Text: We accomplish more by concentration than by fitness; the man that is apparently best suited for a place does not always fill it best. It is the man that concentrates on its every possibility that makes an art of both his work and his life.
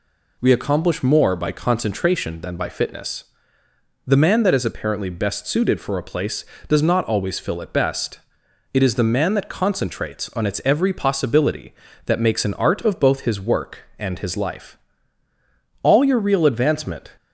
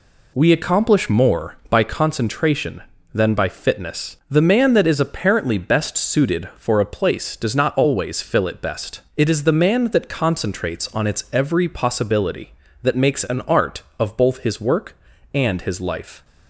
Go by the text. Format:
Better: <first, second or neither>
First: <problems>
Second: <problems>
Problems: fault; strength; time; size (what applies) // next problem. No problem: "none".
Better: second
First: goes on to say "All your real advancement"; from 15.8 s on; 1.3 s long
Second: none